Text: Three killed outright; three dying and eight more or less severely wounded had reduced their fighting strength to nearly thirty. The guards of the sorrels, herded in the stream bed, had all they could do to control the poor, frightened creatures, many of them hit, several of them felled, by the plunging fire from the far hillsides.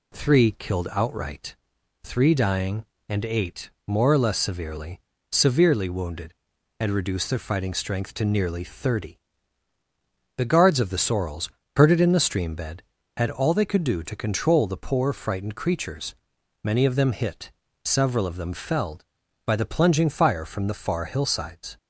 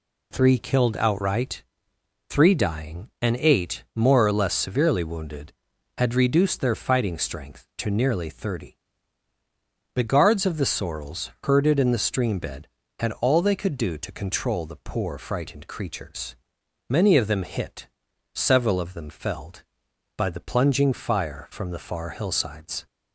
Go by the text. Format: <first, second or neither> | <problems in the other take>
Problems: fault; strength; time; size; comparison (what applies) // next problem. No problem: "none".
second | pauses between "eight" and "more"; slight; at 3.7 s; 0.16 s long // says "severely" twice; at 5.3 s